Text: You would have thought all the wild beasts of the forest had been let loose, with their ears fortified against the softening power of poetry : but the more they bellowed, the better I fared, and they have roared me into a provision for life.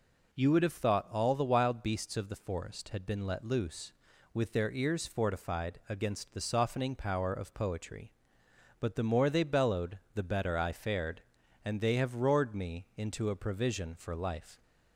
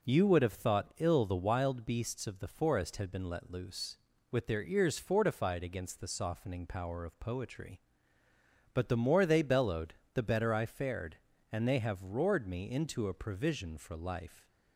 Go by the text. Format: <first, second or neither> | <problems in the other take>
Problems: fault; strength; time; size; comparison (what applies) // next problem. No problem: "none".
first | says "ill" for "all"; at 0.9 s